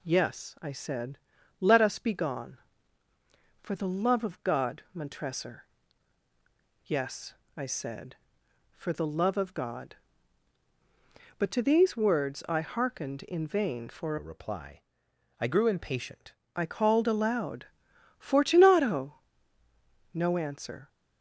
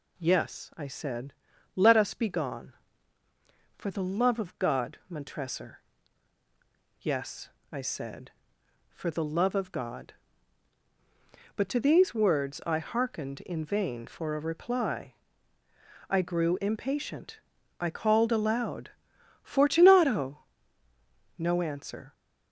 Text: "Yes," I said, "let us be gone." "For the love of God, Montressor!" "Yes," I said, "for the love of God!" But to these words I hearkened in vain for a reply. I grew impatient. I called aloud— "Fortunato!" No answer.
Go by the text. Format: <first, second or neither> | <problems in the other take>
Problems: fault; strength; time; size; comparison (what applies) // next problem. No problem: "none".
second | changes voice from "a" to "impatient"; from 14.1 to 16.3 s; 2.2 s long